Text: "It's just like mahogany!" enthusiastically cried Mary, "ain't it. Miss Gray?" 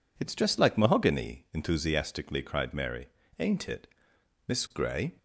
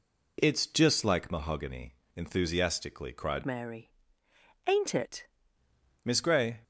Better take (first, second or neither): first